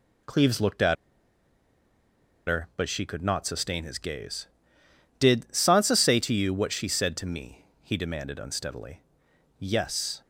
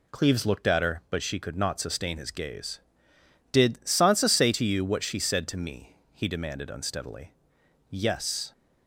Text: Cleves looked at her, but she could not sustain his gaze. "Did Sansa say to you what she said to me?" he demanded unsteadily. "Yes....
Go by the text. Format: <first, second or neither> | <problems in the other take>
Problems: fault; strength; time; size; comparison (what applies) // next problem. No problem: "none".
second | pauses between "at" and "her"; strong; at 0.9 s; 1.5 s long